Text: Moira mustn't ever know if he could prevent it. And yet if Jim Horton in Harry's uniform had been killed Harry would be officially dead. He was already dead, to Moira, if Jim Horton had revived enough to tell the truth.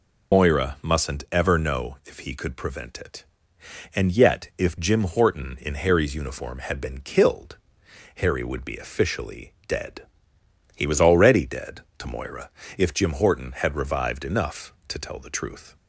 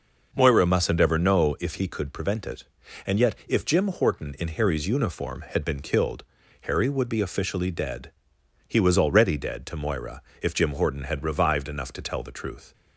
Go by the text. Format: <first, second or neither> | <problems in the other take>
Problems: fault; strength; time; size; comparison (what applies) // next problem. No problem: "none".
second | loses the start of "Moira"; at 0.3 s; 90 ms // pauses between "killed" and "Harry"; noticeable; at 7.5 s; 0.58 s long; also in the second // pauses between "officially" and "dead"; slight; at 9.5 s; 0.16 s long